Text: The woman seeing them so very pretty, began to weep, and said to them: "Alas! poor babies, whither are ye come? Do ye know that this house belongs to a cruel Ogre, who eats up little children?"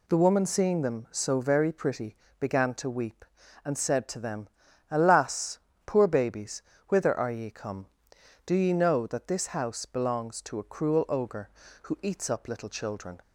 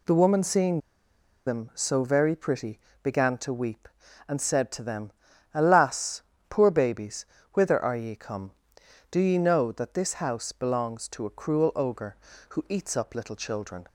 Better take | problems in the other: first | pauses between "seeing" and "them"; noticeable; at 0.7 s; 0.67 s long

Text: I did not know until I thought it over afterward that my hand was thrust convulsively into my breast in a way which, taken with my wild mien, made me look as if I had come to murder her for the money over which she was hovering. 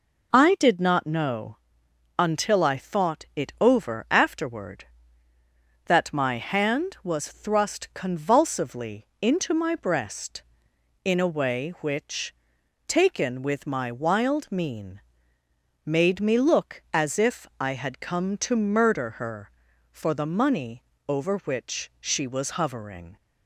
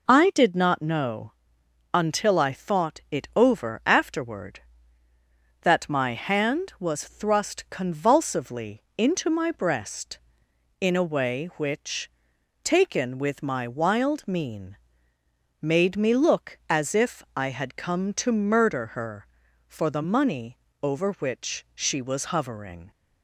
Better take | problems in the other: neither | pauses between "know" and "until"; noticeable; the same in both // pauses between "money" and "over"; slight; the same in both

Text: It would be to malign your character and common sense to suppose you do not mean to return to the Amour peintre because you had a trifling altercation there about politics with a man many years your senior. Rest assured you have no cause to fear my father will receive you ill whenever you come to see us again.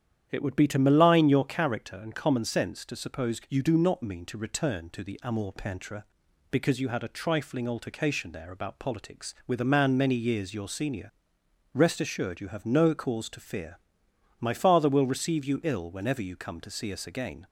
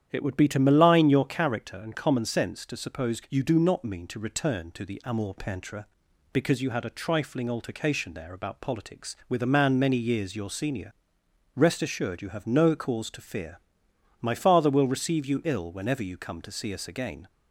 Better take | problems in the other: neither | starts louder than the rest; strong; the same in both // pauses between "fear" and "my"; noticeable; the same in both

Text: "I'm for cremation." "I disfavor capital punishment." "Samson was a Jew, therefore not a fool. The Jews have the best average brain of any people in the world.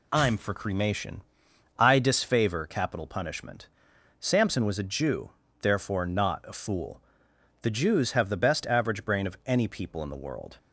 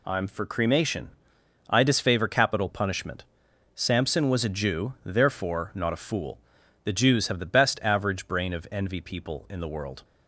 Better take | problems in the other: first | says "envy" for "any"; at 8.7 s

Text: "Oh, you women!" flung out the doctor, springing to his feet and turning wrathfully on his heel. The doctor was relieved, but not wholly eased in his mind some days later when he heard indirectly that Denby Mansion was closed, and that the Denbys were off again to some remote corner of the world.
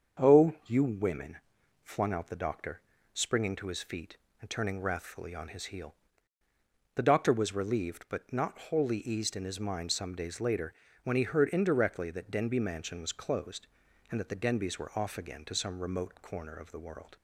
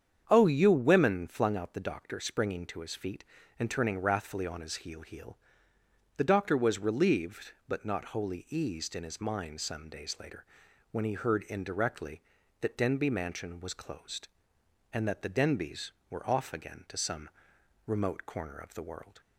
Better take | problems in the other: first | starts louder than the rest; strong; until 1.3 s; 8 dB; also in the first // says "heel" twice; at 5.0 s // pauses between "later" and "when"; noticeable; at 10.4 s; 0.46 s long; slight in the first // pauses between "some" and "remote"; noticeable; at 17.2 s; 0.58 s long

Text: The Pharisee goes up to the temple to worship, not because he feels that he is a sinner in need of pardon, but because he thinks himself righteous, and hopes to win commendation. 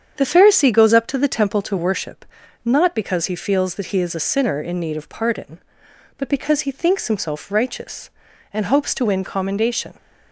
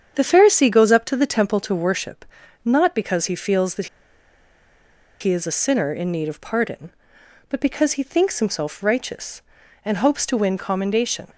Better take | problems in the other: first | starts louder than the rest; strong; until 1.1 s; 8 dB; strong in the first // pauses between "that" and "he"; strong; at 3.8 s; 1.3 s long

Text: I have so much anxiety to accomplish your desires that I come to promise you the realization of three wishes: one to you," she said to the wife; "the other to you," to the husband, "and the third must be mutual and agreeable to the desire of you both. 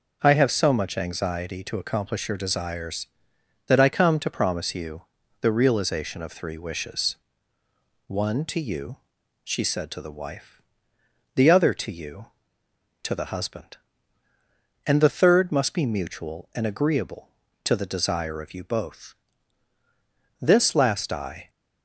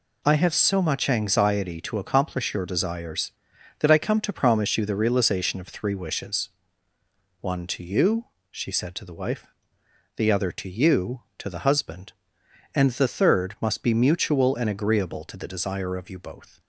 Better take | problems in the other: second | starts louder than the rest; noticeable; until 1.2 s; 6 dB // pauses between "you" and "the"; at 5.0 s; 0.40 s long // goes on to say "This last I"; noticeable; from 20.3 s on; 1.1 s long

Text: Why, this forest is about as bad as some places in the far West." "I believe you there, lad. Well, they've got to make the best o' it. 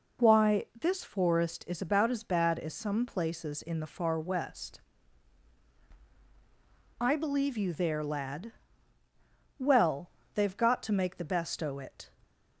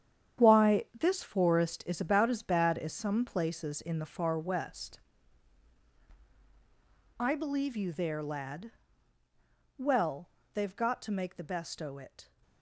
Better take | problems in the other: first | gets quieter; strong; throughout; 10 dB

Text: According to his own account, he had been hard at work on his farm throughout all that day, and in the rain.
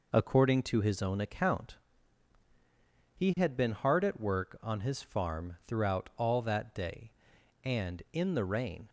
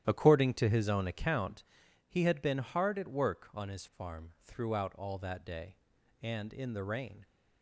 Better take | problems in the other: first | starts louder than the rest; strong; until 1.3 s; 11 dB

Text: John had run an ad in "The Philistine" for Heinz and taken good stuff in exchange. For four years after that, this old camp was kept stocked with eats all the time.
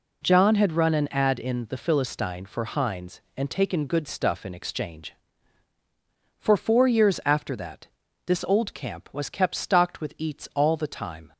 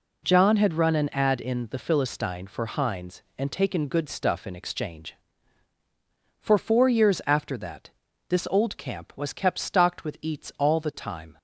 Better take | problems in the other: neither | none

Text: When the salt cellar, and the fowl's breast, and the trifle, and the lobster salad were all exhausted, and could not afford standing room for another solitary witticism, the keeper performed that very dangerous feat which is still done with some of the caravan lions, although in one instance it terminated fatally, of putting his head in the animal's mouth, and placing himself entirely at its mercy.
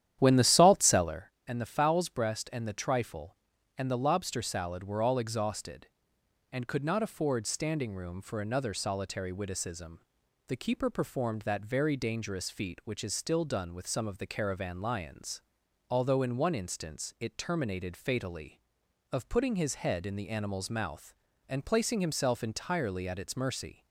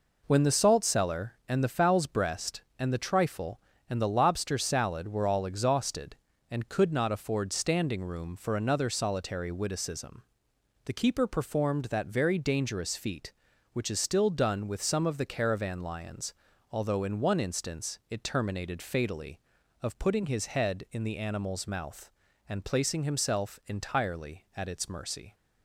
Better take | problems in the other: second | starts louder than the rest; strong; until 1.3 s; 11 dB

